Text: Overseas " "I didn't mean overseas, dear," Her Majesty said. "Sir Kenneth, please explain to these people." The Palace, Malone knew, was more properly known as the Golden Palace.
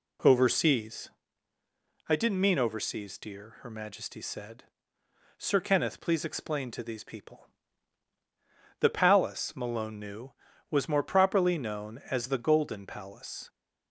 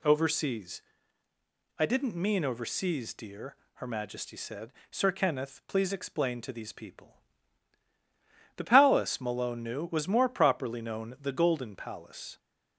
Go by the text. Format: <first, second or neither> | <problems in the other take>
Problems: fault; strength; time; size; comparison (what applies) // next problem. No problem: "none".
first | skips "as"; at 11.1 s